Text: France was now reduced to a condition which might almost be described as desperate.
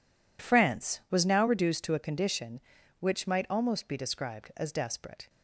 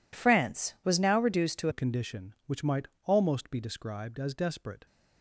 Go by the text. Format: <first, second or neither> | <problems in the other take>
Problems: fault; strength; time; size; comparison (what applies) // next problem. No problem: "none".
first | changes voice at "a"; from 1.6 s on; 3.2 s long // pauses between "might" and "almost"; slight; at 2.8 s; 0.20 s long